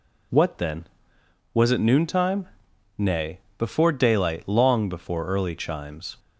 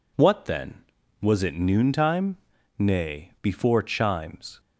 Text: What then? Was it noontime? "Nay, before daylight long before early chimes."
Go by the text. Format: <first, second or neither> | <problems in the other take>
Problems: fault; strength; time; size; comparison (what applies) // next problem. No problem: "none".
first | skips "daylight long before early"; at 3.8 s